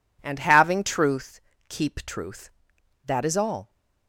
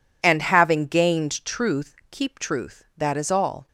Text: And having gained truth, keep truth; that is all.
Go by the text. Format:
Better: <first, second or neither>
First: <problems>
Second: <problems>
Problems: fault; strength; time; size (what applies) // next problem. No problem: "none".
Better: second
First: skips "gained"; at 0.8 s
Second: none